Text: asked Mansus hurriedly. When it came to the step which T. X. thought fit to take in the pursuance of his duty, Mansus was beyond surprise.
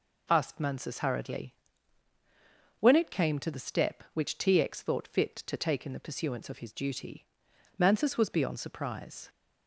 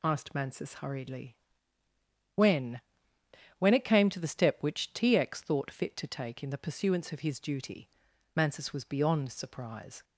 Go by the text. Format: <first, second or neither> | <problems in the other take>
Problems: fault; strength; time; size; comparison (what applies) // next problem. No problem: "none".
first | says "When" twice; at 3.5 s